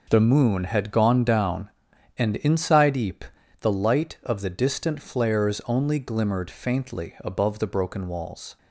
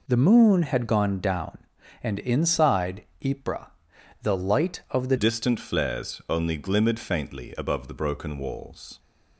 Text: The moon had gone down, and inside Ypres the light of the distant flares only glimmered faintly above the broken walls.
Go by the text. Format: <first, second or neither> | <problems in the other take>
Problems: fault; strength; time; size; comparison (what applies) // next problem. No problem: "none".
first | pauses between "inside" and "Ypres"; slight; at 3.0 s; 0.20 s long // pauses between "Ypres" and "the"; noticeable; at 3.6 s; 0.56 s long; slight in the first // changes voice at "distant"; from 5.1 s on; 3.8 s long